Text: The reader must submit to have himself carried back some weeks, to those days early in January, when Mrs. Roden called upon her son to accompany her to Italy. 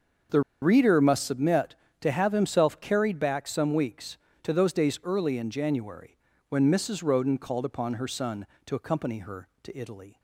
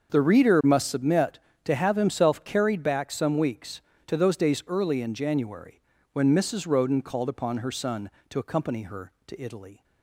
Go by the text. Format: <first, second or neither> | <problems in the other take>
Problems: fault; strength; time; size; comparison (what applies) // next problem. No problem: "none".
second | starts louder than the rest; until 1.5 s; 6.5 dB; also in the second // pauses between "The" and "reader"; slight; at 0.4 s; 0.21 s long